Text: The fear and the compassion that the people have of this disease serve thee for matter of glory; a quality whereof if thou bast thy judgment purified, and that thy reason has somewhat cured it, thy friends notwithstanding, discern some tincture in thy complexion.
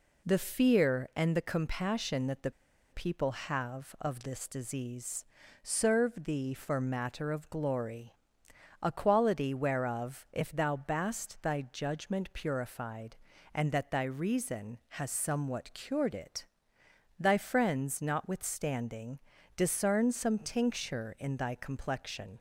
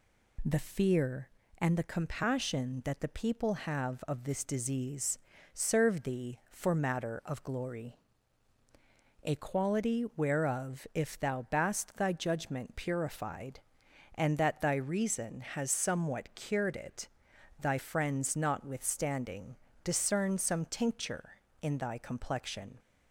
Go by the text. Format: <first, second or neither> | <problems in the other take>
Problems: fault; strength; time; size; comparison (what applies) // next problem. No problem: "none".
second | pauses between "the" and "people"; at 2.5 s; 0.40 s long // pauses between "disease" and "serve"; at 5.2 s; 0.40 s long; slight in the second